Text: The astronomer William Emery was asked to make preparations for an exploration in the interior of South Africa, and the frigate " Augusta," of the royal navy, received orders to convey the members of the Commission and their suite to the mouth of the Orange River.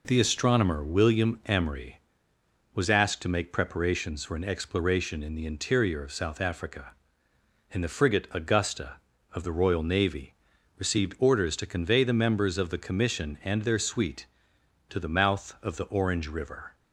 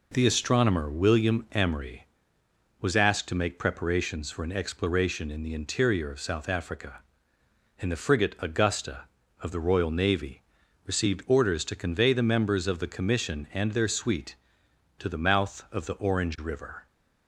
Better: neither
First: none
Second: none

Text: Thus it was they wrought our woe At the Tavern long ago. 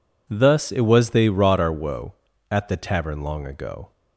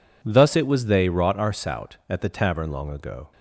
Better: first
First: none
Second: says "sout" for "woe"; at 1.5 s

